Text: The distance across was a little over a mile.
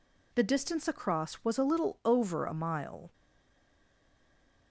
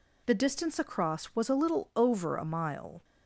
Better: second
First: stays silent after the last word; noticeable; from 3.1 s on; 1.6 s long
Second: none

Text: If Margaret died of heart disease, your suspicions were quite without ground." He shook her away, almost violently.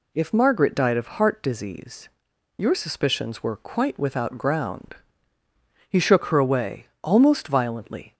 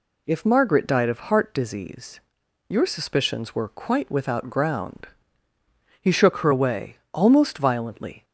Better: neither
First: none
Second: none

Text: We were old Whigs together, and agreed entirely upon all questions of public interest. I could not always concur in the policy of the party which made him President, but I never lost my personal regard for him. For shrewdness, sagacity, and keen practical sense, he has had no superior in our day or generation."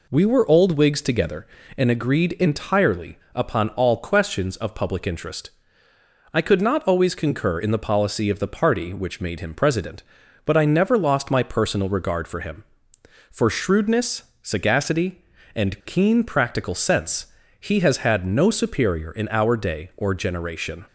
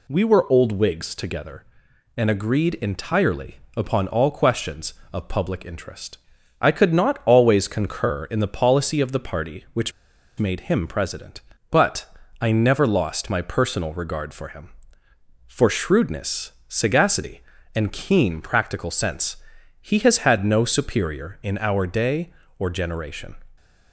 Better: first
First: pauses between "entirely" and "upon"; slight; at 3.1 s; 0.16 s long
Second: pauses between "entirely" and "upon"; slight; at 3.5 s; 0.20 s long // pauses between "which" and "made"; noticeable; at 9.9 s; 0.47 s long // pauses between "but" and "I"; slight; at 12.0 s; 0.34 s long

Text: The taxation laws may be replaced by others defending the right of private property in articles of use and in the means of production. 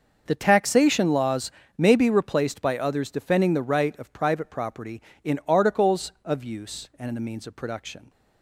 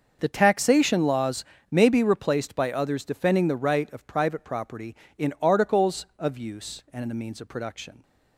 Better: neither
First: starts louder than the rest; until 1.2 s; 6 dB // pauses between "laws" and "may"; slight; at 1.5 s; 0.26 s long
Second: starts louder than the rest; until 1.2 s; 6 dB // pauses between "laws" and "may"; slight; at 1.4 s; 0.26 s long

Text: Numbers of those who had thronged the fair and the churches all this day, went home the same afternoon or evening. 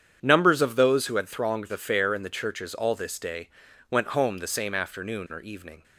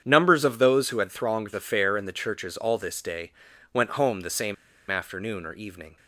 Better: first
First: starts louder than the rest; strong; until 1.2 s; 8.5 dB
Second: starts louder than the rest; strong; until 1.0 s; 8.5 dB // pauses between "same" and "afternoon"; slight; at 4.5 s; 0.35 s long

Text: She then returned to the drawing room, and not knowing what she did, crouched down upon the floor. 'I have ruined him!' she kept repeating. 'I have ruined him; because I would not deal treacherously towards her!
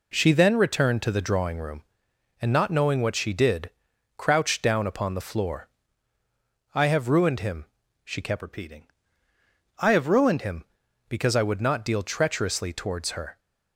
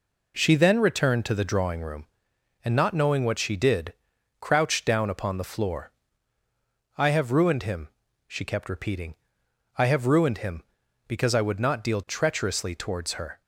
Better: second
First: changes voice from "repeating" to "ruined"; from 8.4 to 10.4 s; 2.0 s long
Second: none

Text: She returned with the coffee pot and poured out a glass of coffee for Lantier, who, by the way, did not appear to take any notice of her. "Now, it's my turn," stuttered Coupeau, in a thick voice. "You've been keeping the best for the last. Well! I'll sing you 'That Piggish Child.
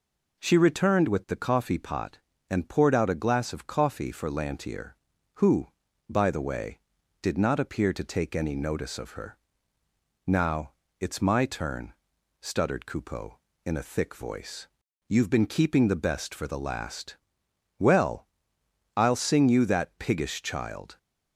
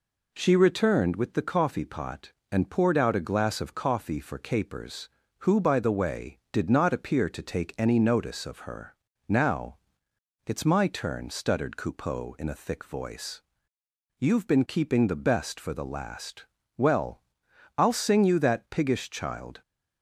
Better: first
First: none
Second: says "Capers" for "Lantier"; at 4.3 s

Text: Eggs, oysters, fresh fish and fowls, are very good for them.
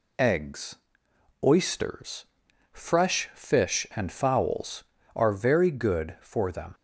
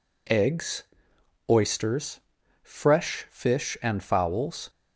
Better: first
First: none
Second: stops before "are very good for them"; at 4.6 s

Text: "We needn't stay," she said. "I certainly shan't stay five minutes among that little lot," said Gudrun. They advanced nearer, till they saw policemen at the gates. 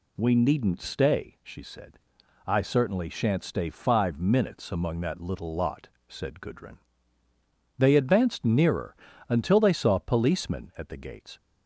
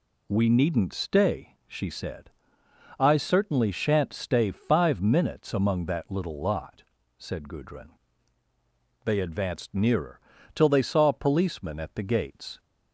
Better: second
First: says "until" for "till"; at 9.2 s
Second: none

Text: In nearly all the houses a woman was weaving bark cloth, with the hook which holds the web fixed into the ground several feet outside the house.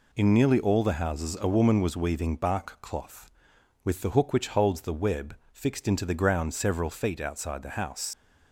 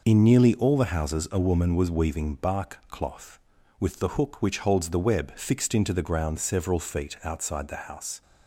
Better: second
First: pauses between "web" and "fixed"; slight; at 5.3 s; 0.18 s long // leaves "house" unfinished; at 8.1 s; 85 ms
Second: none

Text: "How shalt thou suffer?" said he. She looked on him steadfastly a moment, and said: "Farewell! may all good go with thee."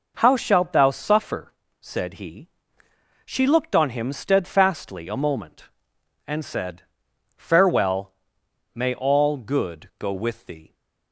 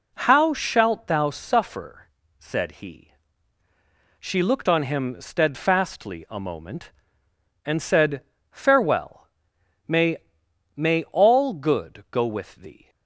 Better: first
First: none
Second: says "may" twice; at 10.7 s

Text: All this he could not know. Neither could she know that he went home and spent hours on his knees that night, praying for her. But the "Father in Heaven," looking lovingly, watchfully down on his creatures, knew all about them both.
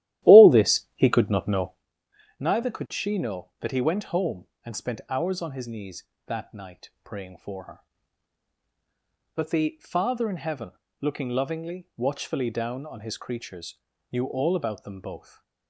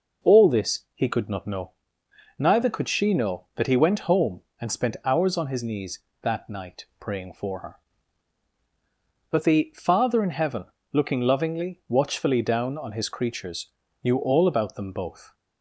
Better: second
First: starts louder than the rest; strong; until 1.9 s; 13.5 dB // stays silent after the last word; slight; from 15.1 s on; 0.5 s long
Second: none

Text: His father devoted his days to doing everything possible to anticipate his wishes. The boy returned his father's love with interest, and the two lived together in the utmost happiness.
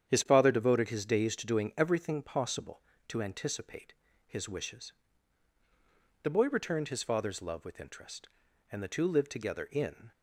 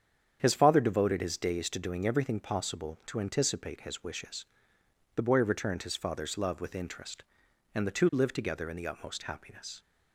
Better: second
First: starts louder than the rest; strong; until 1.1 s; 9 dB // pauses between "anticipate" and "his"; slight; at 3.9 s; 0.32 s long // stops before "the utmost happiness"; at 10.1 s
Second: starts louder than the rest; strong; until 1.4 s; 8.5 dB

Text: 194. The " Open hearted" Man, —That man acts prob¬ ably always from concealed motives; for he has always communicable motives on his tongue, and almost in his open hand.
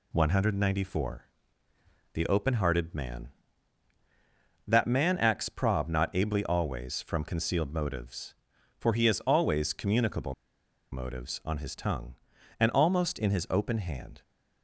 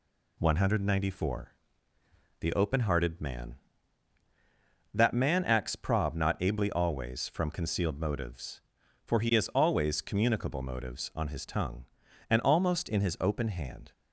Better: second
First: pauses between "communicable" and "motives"; noticeable; at 10.3 s; 0.57 s long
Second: none

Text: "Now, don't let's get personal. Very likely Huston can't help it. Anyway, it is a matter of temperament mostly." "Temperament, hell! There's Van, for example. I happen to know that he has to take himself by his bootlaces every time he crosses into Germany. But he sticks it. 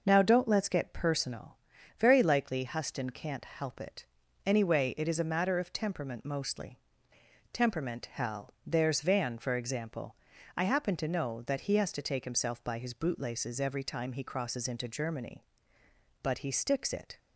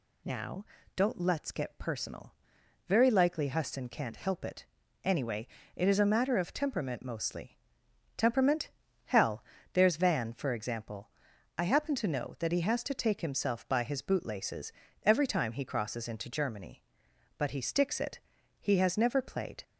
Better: first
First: none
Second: pauses between "bootlaces" and "every"; slight; at 14.7 s; 0.32 s long // goes on to say "He has never played"; noticeable; from 18.6 s on; 1.0 s long

